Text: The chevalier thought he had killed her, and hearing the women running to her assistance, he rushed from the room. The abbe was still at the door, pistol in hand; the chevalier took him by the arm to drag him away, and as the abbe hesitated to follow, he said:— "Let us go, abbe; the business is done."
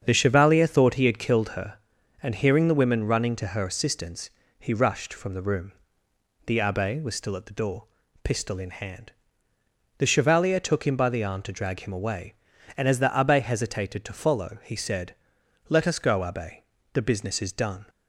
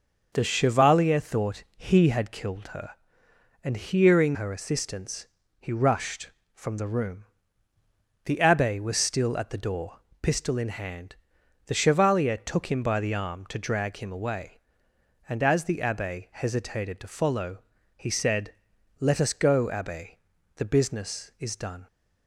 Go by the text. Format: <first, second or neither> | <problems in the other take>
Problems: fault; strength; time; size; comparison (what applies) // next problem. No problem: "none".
first | starts louder than the rest; noticeable; until 1.3 s; 6 dB; strong in the first // skips "the women running to"; at 4.3 s